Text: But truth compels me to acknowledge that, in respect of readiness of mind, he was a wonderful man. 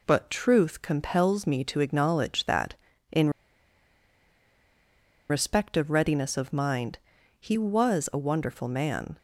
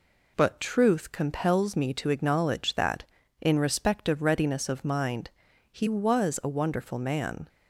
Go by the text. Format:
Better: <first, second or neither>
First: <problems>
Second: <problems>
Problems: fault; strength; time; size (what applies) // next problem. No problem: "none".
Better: second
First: pauses between "in" and "respect"; strong; at 3.2 s; 2.0 s long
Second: none